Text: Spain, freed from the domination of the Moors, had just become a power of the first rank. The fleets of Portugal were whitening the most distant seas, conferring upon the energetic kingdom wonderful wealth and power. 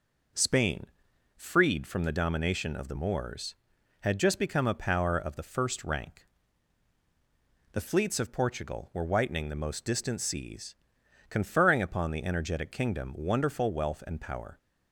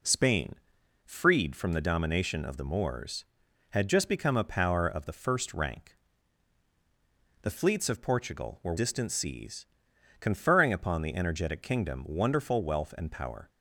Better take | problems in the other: first | skips "whitening the most"; at 8.7 s

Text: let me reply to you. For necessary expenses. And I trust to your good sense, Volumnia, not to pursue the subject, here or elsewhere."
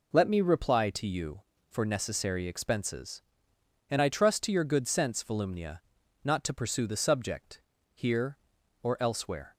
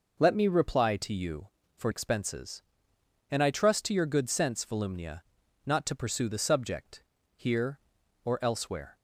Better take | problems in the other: first | skips "necessary"; at 1.9 s

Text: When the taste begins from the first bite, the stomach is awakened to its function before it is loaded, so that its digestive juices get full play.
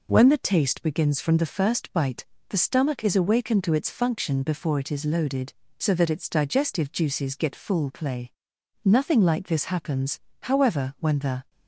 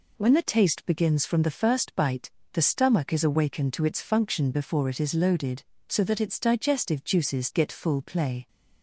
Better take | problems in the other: second | goes on to say "Nothing like this happens however when the"; strong; from 8.8 s on; 2.6 s long

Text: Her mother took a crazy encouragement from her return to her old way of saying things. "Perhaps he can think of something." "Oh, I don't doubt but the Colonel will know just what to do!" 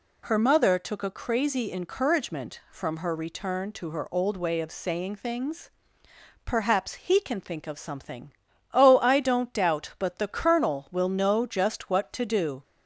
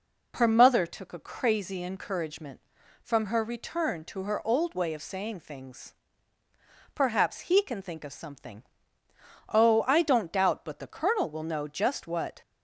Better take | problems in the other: first | stops before "to do"; at 12.4 s

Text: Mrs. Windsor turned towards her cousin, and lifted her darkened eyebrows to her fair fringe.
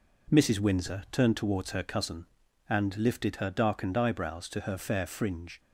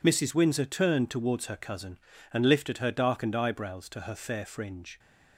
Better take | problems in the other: neither | none

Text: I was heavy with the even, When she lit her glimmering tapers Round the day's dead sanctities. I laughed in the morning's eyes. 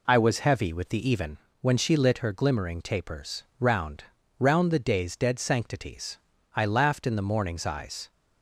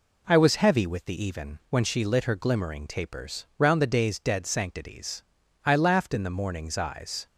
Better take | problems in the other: second | pauses between "tapers" and "Round"; slight; at 3.4 s; 0.16 s long // says "Round" twice; at 4.3 s

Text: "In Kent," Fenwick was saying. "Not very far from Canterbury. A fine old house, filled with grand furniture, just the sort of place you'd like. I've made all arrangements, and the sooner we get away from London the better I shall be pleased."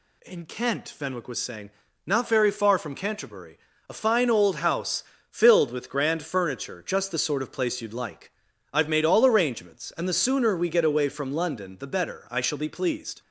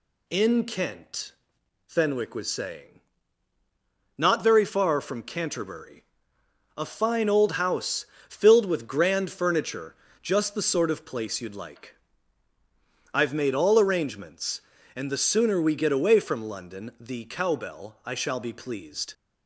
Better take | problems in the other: first | says "cowbell" for "better"; at 17.2 s

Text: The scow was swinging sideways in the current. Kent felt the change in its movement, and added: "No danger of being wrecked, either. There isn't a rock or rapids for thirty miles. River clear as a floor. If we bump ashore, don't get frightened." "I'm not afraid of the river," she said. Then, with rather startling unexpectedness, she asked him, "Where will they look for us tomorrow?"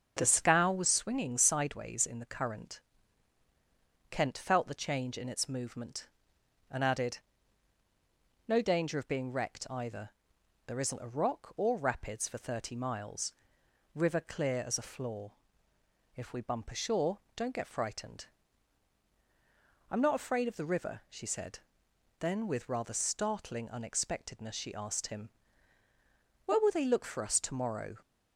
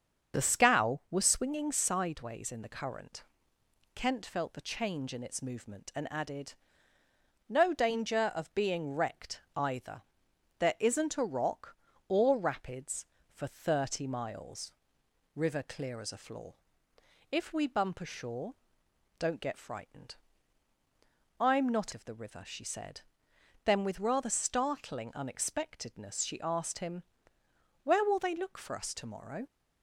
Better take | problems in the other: first | starts louder than the rest; strong; until 1.4 s; 7 dB; also in the first // skips "afraid"; at 21.9 s

